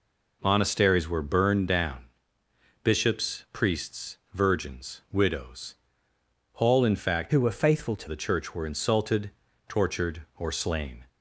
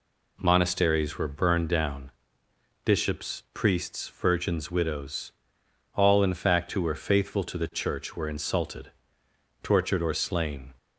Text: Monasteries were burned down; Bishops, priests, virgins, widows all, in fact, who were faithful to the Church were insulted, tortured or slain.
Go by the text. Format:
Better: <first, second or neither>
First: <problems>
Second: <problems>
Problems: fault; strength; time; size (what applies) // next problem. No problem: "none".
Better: second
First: pauses between "widows" and "all"; noticeable; at 5.7 s; 0.80 s long // changes voice from "who" to "to"; from 7.2 to 8.0 s; 0.8 s long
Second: pauses between "widows" and "all"; noticeable; at 5.3 s; 0.64 s long